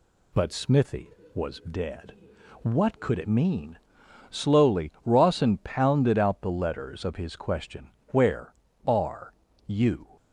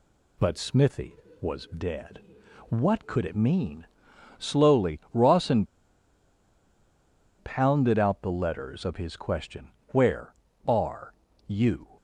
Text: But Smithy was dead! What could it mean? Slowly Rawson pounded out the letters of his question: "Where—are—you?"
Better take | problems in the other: first | pauses between "Rawson" and "pounded"; strong; at 5.6 s; 1.7 s long

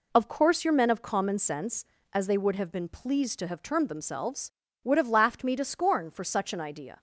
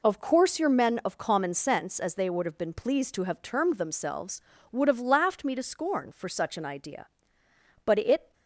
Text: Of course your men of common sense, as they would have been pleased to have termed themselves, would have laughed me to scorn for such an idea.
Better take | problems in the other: first | goes on to say "But it"; slight; from 7.8 s on; 0.48 s long

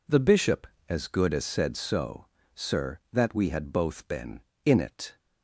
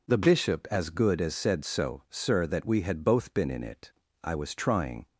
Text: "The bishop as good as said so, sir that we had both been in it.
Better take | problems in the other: first | goes on to say "I was trying"; noticeable; from 4.2 s on; 0.82 s long

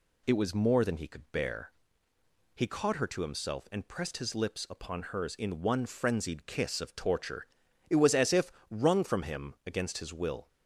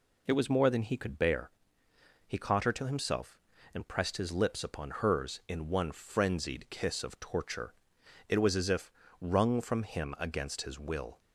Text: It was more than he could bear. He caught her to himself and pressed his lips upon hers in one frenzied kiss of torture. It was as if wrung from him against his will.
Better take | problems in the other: neither | pauses between "if" and "wrung"; slight; the same in both

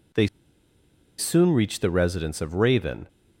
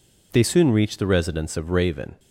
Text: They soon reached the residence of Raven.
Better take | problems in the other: second | pauses between "They" and "soon"; noticeable; at 0.2 s; 0.92 s long

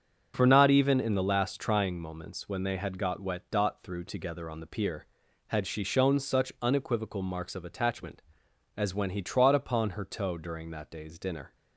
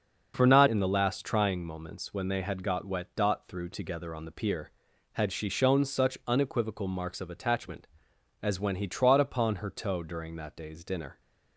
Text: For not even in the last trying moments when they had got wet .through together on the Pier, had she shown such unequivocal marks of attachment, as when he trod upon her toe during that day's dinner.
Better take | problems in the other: first | starts louder than the rest; noticeable; until 1.3 s; 6 dB; also in the first // skips "even"; at 0.6 s

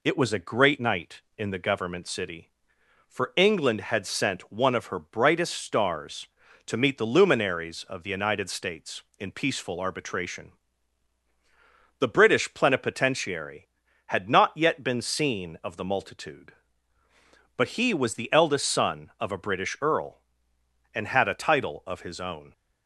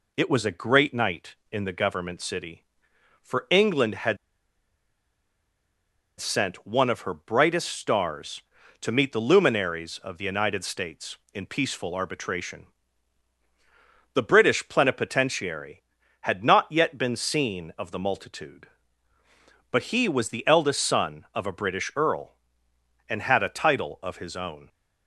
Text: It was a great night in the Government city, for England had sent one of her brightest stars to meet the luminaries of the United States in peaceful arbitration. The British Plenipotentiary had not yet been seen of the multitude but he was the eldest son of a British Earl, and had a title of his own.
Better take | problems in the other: first | pauses between "had" and "sent"; strong; at 4.1 s; 2.0 s long

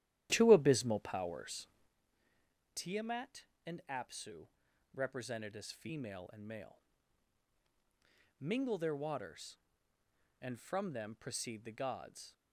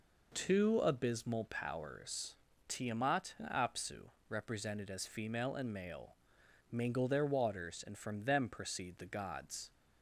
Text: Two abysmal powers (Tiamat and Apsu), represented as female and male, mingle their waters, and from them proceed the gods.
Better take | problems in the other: second | starts louder than the rest; strong; until 2.0 s; 12.5 dB

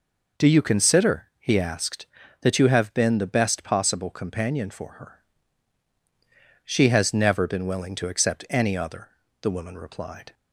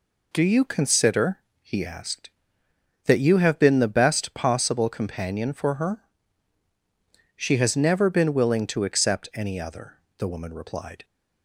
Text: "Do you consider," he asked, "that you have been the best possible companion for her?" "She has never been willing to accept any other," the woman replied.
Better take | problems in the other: neither | none

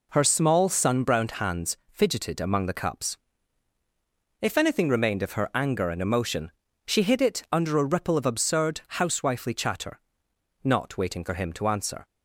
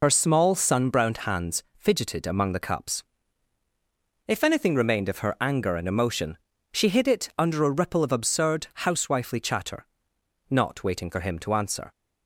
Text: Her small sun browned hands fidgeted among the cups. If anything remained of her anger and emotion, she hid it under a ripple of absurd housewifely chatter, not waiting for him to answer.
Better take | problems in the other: first | loses the start of "Her"; at 0.0 s; 60 ms // pauses between "hands" and "fidgeted"; slight; at 1.6 s; 0.16 s long; slight in the first // pauses between "absurd" and "housewifely"; slight; at 8.6 s; 0.18 s long; slight in the first

